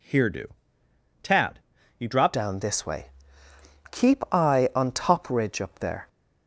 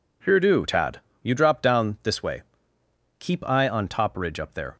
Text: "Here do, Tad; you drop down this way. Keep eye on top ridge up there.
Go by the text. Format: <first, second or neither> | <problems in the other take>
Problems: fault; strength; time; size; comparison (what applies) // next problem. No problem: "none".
second | changes voice at "down"; from 2.3 s on; 3.7 s long